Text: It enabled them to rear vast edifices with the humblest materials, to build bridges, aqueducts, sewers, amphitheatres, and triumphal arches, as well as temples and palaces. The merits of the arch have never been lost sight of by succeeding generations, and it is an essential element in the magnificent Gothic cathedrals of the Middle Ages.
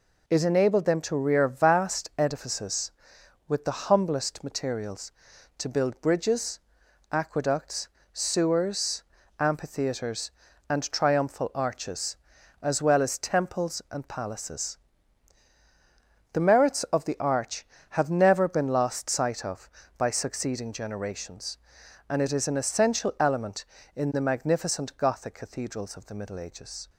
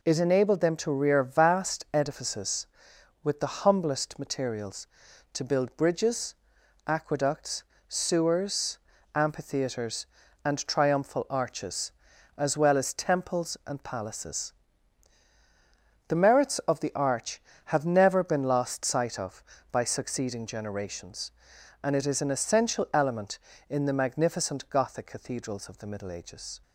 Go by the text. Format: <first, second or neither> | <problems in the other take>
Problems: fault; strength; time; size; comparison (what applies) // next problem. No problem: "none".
neither | none